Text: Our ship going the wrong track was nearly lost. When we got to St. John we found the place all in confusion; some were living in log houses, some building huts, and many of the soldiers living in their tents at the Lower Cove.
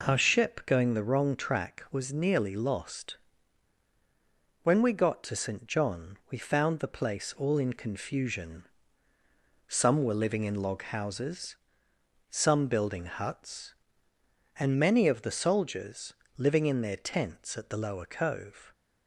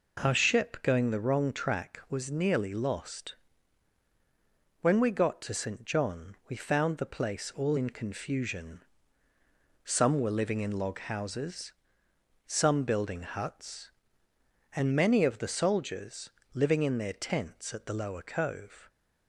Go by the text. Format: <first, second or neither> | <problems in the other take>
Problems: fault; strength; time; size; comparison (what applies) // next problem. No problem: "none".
neither | pauses between "soldiers" and "living"; slight; the same in both